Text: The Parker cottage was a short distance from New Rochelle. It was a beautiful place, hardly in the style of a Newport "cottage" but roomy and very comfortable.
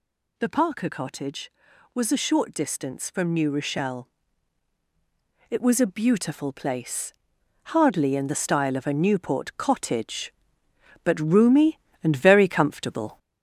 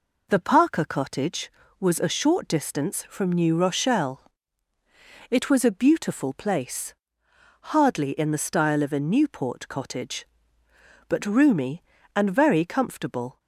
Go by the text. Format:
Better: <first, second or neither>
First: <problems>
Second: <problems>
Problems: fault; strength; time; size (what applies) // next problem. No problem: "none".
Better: second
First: gets louder; slight; throughout; 3 dB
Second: none